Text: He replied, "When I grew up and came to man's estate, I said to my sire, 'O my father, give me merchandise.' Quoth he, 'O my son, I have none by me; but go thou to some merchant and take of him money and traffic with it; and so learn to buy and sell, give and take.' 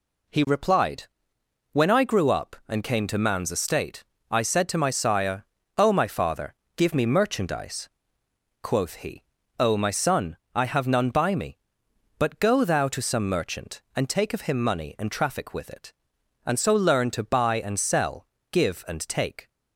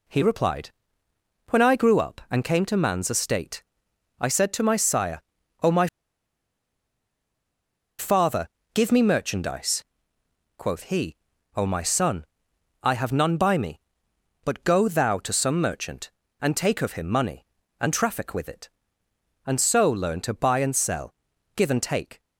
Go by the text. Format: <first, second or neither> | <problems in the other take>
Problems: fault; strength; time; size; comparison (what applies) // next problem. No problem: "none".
first | pauses between "my" and "father"; strong; at 5.8 s; 2.1 s long